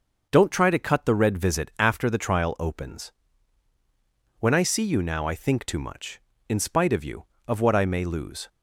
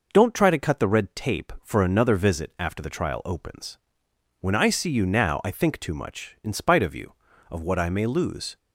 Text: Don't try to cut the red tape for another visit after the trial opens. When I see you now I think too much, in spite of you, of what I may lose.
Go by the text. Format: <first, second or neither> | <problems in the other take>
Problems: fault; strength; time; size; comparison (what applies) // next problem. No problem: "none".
second | starts louder than the rest; noticeable; until 1.3 s; 6 dB // skips "tape for another"; at 1.3 s